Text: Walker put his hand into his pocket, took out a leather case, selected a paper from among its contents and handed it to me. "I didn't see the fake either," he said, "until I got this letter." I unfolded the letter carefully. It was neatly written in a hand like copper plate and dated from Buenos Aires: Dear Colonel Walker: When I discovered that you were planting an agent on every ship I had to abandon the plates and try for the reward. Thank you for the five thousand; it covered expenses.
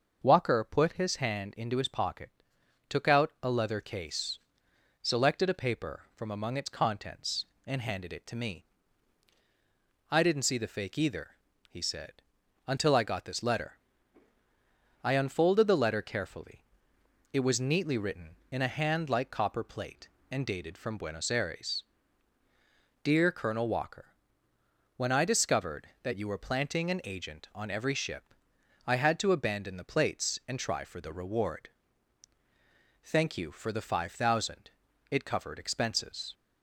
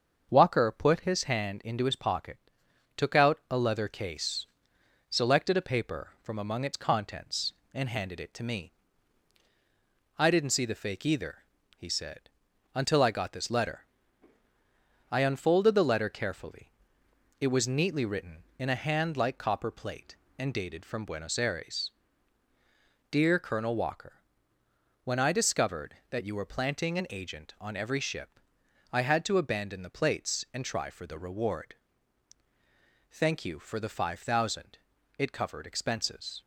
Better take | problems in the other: first | gets quieter; throughout; 3.5 dB // starts louder than the rest; until 1.3 s; 6.5 dB; also in the first // pauses between "ship" and "I"; noticeable; at 28.4 s; 0.50 s long; noticeable in the first

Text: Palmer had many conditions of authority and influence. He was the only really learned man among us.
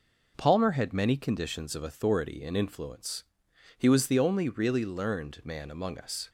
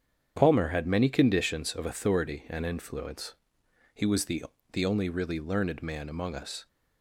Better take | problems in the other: first | starts louder than the rest; strong; until 1.3 s; 8 dB // says "the" twice; at 4.7 s

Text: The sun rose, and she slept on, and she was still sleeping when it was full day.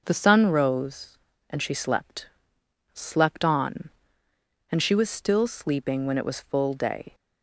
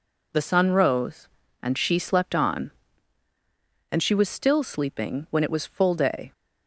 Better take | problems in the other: second | starts louder than the rest; until 1.0 s; 6 dB // says "slept" twice; at 2.9 s

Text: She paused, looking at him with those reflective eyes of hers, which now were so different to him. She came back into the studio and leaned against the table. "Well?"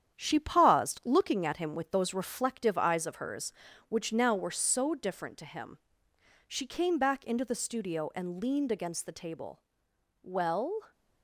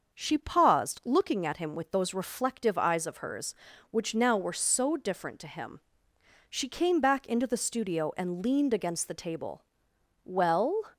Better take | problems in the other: second | gets quieter; noticeable; throughout; 5 dB // starts louder than the rest; strong; until 1.2 s; 9 dB; also in the second

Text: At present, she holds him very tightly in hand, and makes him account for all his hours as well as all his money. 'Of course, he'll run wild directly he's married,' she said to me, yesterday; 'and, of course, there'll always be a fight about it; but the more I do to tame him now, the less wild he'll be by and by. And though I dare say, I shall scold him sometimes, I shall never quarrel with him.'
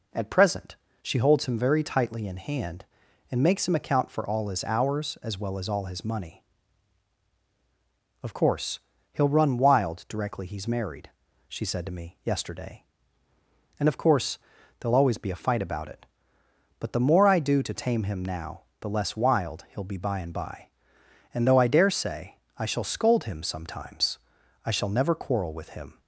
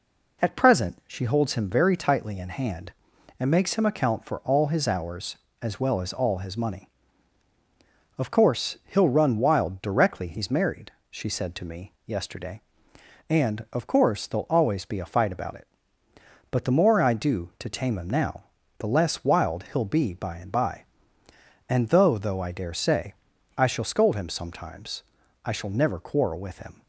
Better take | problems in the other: first | says "though" twice; at 22.1 s

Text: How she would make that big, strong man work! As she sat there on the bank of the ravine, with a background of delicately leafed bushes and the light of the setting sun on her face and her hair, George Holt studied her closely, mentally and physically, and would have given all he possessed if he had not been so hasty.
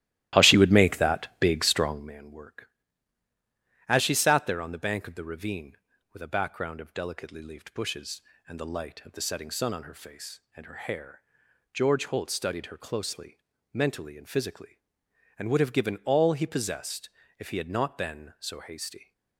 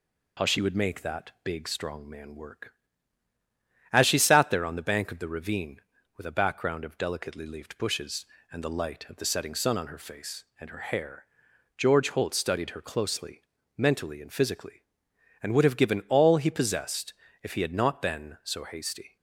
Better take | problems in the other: second | starts louder than the rest; strong; until 2.2 s; 14.5 dB // pauses between "possessed" and "if"; slight; at 17.0 s; 0.28 s long; slight in the second

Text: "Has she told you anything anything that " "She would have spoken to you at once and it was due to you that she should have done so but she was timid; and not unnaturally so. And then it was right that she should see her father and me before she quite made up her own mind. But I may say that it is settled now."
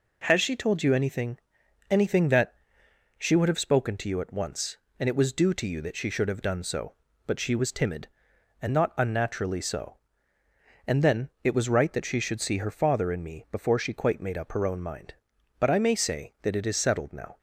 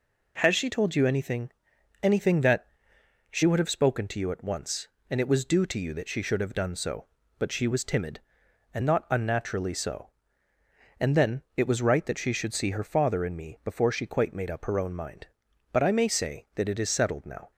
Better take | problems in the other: neither | pauses between "anything" and "anything"; noticeable; the same in both

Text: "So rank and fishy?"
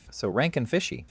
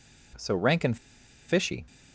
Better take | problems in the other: first | pauses between "and" and "fishy"; noticeable; at 0.9 s; 0.51 s long

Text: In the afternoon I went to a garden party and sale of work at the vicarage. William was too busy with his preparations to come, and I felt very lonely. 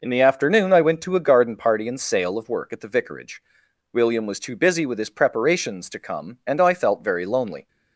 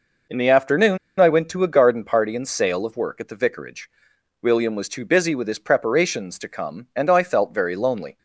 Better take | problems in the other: first | pauses between "afternoon" and "I"; slight; at 0.9 s; 0.21 s long

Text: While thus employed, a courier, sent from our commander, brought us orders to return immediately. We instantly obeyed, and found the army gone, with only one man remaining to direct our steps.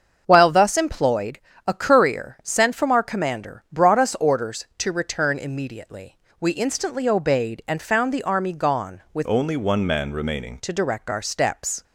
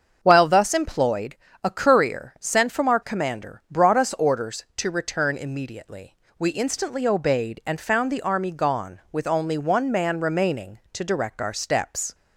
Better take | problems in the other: second | starts louder than the rest; until 1.2 s; 7 dB; also in the second // changes voice from "only" to "remaining"; from 9.2 to 10.5 s; 1.3 s long

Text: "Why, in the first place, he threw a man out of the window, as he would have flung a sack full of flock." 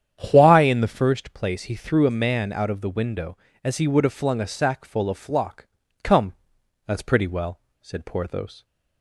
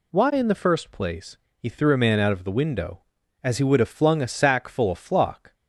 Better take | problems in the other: second | starts louder than the rest; strong; until 1.3 s; 9 dB // goes on to say "Come that's pretty well said Porthos"; strong; from 6.0 s on; 2.6 s long

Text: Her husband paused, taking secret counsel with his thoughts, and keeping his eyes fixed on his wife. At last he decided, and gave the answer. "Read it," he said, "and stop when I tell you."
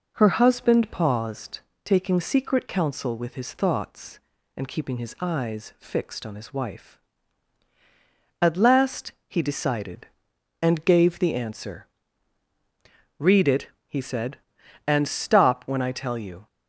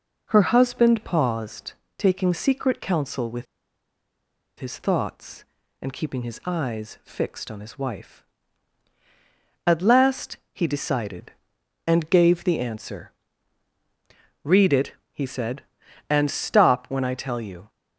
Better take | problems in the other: first | pauses between "with" and "his"; at 3.4 s; 1.1 s long // pauses between "last" and "he"; slight; at 10.3 s; 0.16 s long; slight in the first

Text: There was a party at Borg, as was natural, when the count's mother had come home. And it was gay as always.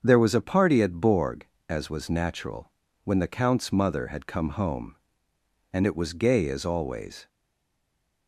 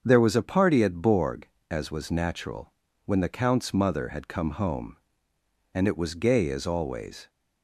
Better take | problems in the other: second | starts louder than the rest; until 1.0 s; 7 dB; also in the second // stays silent after the last word; from 7.2 s on; 1.0 s long

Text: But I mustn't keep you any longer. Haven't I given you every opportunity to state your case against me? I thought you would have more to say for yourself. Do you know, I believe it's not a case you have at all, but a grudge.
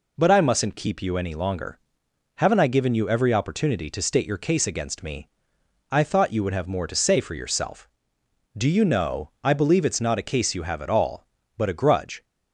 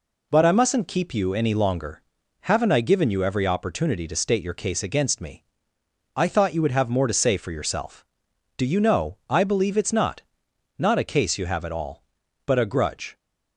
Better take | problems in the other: first | says "not" twice; at 10.7 s

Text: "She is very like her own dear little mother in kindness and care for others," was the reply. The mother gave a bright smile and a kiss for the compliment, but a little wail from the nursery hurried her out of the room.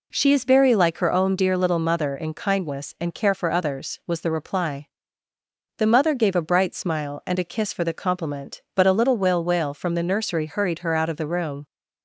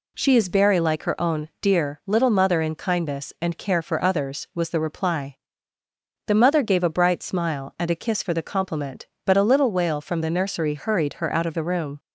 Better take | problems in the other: second | says "wail" twice; at 9.4 s

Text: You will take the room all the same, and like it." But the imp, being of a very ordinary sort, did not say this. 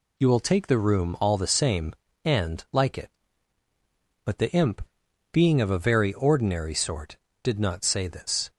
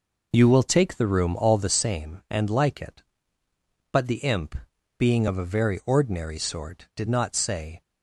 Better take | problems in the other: first | stops before "this"; at 7.8 s

